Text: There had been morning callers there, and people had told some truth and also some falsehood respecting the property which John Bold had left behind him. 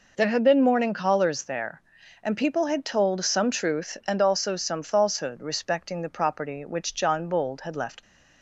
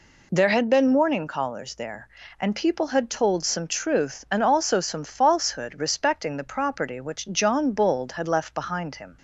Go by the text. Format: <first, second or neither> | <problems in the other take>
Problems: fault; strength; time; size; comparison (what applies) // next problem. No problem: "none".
second | stops before "behind him"; at 8.0 s